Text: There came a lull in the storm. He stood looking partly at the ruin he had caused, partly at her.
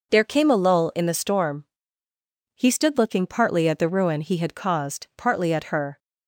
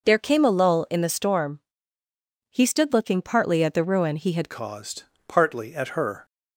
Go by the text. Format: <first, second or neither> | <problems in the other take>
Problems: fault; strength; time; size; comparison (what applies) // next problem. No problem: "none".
first | changes voice at "caused"; from 4.5 s on; 1.7 s long